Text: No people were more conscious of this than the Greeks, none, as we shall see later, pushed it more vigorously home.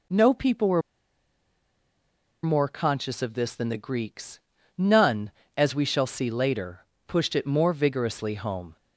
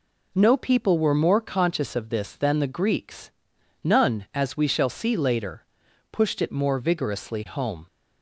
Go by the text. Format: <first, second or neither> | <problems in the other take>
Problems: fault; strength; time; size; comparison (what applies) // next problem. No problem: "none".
second | pauses between "were" and "more"; strong; at 0.8 s; 1.6 s long